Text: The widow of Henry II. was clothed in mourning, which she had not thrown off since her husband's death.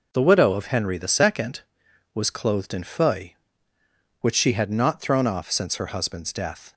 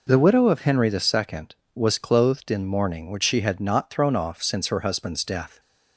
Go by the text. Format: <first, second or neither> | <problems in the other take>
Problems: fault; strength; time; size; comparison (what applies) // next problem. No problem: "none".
second | says "feuille" for "mourning"; at 2.8 s